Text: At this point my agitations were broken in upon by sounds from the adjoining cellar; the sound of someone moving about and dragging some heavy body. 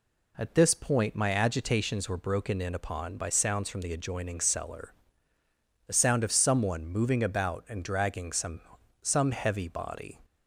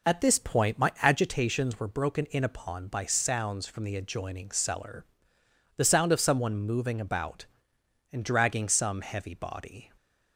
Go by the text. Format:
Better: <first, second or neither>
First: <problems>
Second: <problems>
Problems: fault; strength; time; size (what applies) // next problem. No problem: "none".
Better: second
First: says "some" twice; at 9.0 s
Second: none